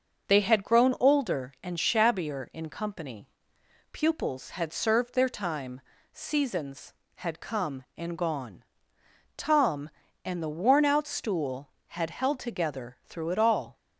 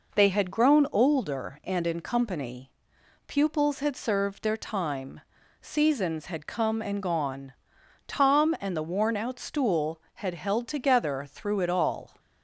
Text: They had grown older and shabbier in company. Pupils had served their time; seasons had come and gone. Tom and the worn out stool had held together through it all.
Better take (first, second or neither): first